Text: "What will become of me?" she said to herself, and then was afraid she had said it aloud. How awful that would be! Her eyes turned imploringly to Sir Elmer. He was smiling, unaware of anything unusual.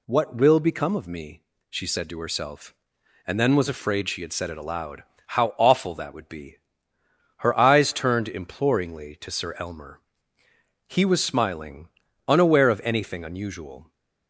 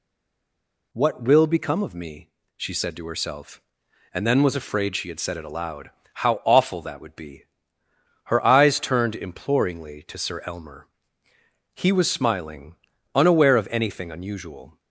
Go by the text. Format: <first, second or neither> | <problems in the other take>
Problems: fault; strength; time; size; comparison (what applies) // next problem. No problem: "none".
first | stays silent before the first word; slight; until 0.9 s; 0.9 s long